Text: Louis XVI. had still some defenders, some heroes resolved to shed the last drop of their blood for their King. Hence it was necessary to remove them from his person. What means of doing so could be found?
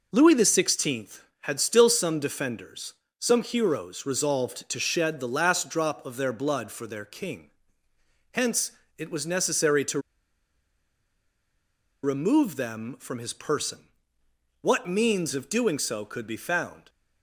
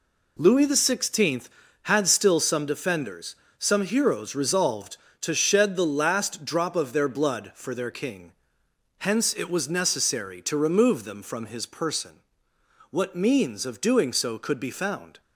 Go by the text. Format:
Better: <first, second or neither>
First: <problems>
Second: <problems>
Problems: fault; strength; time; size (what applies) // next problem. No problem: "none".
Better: second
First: pauses between "Hence" and "it"; slight; at 8.7 s; 0.26 s long // pauses between "to" and "remove"; strong; at 9.9 s; 2.0 s long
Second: none